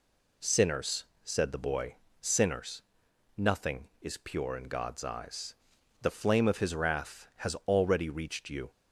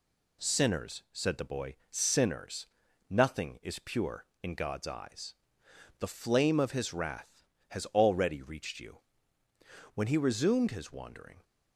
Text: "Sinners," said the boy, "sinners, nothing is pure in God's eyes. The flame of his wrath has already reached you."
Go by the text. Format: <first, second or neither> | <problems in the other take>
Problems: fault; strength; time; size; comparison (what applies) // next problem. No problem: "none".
first | goes on to say "When he resumed his wandering"; from 9.9 s on; 1.4 s long